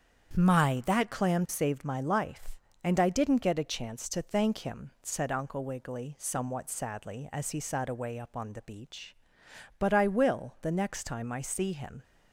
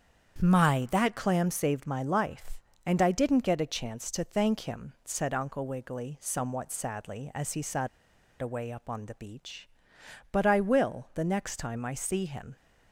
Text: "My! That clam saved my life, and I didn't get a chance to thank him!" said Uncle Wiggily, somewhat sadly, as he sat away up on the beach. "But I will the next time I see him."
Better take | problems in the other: first | starts louder than the rest; strong; until 1.4 s; 8 dB; strong in the first // pauses between "sat" and "away"; noticeable; at 7.8 s; 0.53 s long

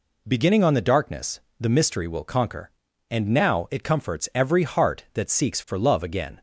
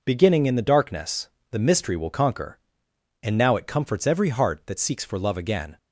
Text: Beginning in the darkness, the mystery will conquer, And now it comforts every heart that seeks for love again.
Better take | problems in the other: second | says "on" for "in"; at 0.6 s

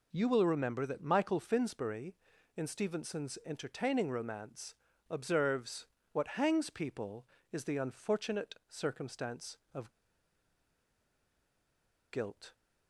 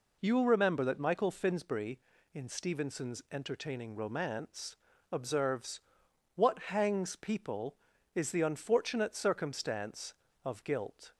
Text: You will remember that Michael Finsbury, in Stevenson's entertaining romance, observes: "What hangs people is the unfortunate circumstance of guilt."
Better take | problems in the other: second | pauses between "of" and "guilt"; strong; at 9.9 s; 2.2 s long

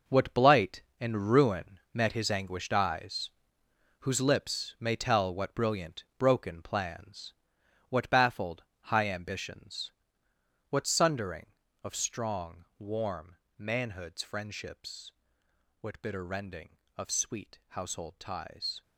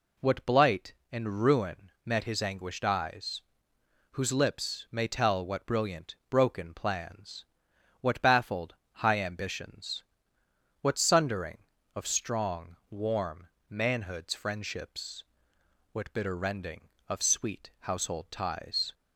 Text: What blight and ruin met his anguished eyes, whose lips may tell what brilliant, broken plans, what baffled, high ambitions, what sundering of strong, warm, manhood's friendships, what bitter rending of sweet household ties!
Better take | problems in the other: second | gets quieter; strong; throughout; 10.5 dB

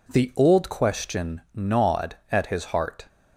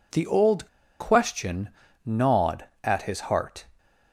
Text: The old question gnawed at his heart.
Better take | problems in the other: first | pauses between "old" and "question"; slight; at 0.6 s; 0.33 s long // pauses between "question" and "gnawed"; slight; at 1.6 s; 0.34 s long

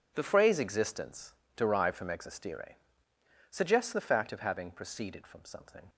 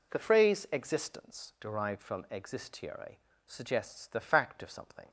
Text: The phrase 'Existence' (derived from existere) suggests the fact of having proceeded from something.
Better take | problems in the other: first | skips "having proceeded from"; at 4.7 s

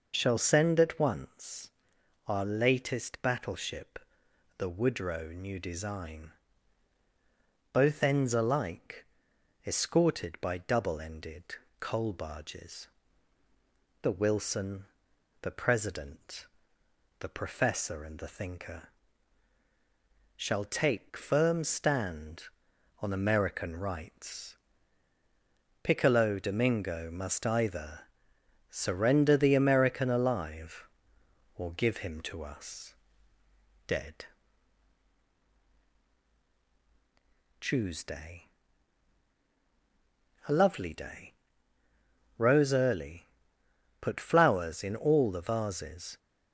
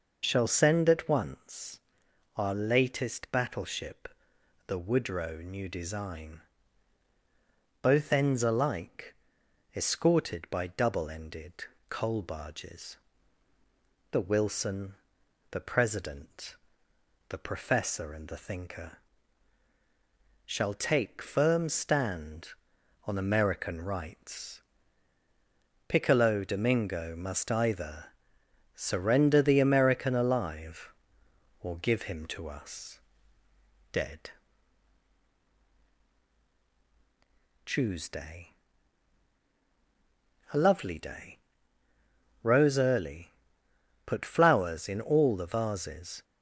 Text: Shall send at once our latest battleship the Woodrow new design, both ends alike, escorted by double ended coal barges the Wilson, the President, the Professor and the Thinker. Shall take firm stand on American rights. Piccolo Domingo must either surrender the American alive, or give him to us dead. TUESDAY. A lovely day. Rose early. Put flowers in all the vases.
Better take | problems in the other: neither | pauses between "once" and "our"; noticeable; the same in both // pauses between "battleship" and "the"; noticeable; the same in both // pauses between "ended" and "coal"; the same in both // pauses between "barges" and "the"; the same in both // pauses between "either" and "surrender"; noticeable; the same in both // pauses between "us" and "dead"; noticeable; the same in both

